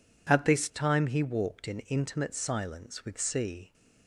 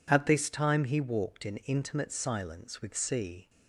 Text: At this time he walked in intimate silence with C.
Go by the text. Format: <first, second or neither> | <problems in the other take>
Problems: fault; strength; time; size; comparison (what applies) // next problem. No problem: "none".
neither | none